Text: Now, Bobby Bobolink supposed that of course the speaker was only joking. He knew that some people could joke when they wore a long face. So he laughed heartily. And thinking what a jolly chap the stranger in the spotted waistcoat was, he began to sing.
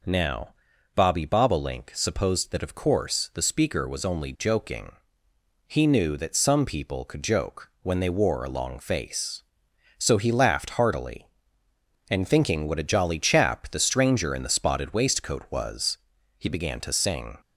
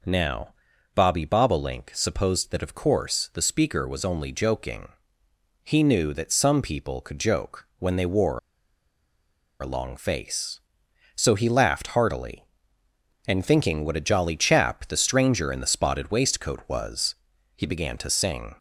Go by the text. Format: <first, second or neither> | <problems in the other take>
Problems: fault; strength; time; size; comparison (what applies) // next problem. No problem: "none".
first | pauses between "wore" and "a"; at 8.3 s; 1.2 s long